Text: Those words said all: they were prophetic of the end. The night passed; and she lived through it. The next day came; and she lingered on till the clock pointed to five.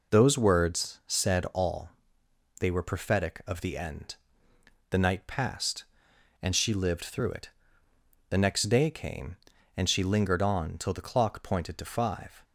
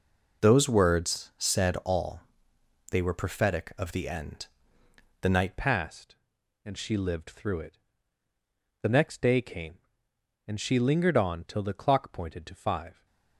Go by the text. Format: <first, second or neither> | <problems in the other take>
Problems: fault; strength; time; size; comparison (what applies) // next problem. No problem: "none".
first | changes voice at "passed"; from 5.5 s on; 7.5 s long